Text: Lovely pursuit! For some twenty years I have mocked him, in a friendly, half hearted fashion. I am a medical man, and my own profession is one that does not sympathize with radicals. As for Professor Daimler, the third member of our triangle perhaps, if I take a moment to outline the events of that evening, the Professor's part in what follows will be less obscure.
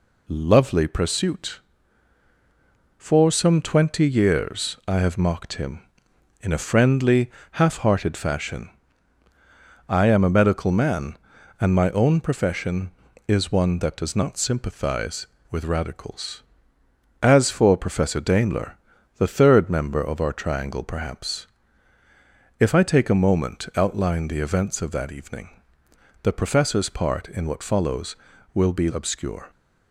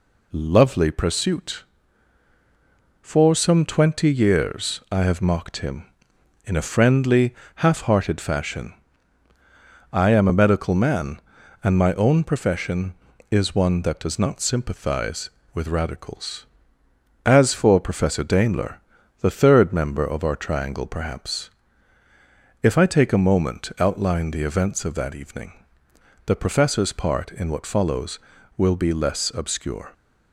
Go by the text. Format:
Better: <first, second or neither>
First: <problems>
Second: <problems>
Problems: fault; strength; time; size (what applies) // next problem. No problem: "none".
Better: second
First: skips "less"; at 28.8 s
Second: none